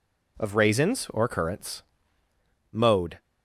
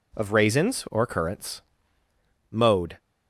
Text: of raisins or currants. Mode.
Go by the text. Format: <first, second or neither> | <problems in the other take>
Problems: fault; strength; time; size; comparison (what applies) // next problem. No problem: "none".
neither | none